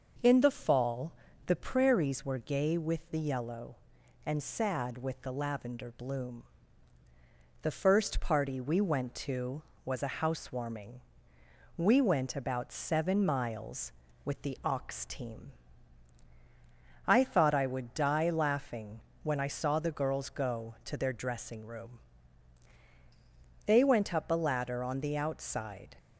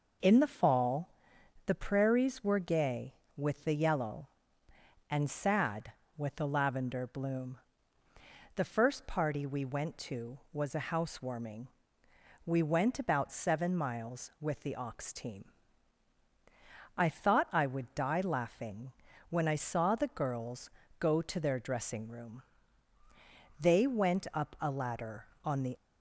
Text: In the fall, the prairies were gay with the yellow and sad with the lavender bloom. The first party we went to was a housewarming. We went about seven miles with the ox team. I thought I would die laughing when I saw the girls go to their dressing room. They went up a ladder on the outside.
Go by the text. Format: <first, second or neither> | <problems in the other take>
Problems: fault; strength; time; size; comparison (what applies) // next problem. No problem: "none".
first | pauses between "laughing" and "when"; at 18.9 s; 0.38 s long; slight in the first // pauses between "girls" and "go"; slight; at 20.6 s; 0.30 s long // stops before "outside"; at 25.7 s